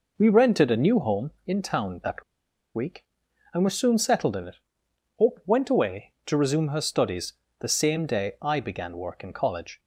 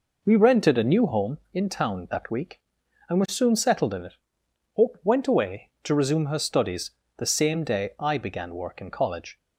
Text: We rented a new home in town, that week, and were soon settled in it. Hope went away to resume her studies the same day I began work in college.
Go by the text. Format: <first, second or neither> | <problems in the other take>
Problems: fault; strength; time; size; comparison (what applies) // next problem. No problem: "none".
second | pauses between "that" and "week"; noticeable; at 2.2 s; 0.51 s long // pauses between "studies" and "the"; slight; at 7.3 s; 0.26 s long; slight in the second